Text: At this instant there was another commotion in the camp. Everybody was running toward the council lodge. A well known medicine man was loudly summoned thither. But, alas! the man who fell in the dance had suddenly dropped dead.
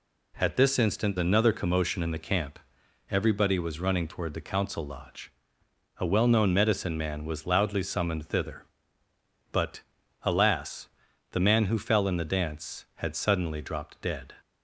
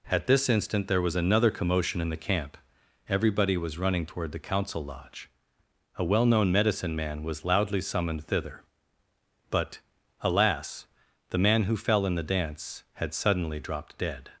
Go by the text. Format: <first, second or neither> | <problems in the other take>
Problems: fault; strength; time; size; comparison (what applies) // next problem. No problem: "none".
second | skips "there was"; at 1.1 s